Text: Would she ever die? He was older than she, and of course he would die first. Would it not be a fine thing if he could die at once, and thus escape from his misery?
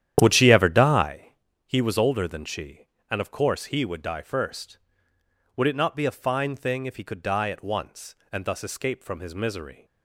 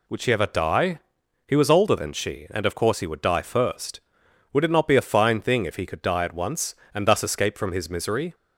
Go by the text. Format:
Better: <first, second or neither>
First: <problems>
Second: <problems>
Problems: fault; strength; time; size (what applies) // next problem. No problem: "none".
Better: second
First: starts louder than the rest; strong; until 1.3 s; 10.5 dB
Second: none